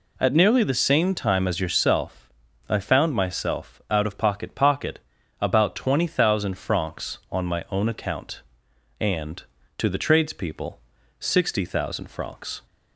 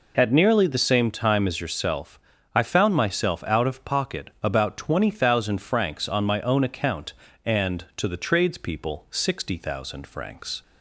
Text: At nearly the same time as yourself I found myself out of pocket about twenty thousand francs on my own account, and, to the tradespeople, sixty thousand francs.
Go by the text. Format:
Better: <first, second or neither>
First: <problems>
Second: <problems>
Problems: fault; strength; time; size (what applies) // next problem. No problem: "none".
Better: second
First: pauses between "yourself" and "I"; at 2.2 s; 0.38 s long // says "pocket" twice; at 4.5 s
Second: pauses between "yourself" and "I"; slight; at 2.1 s; 0.36 s long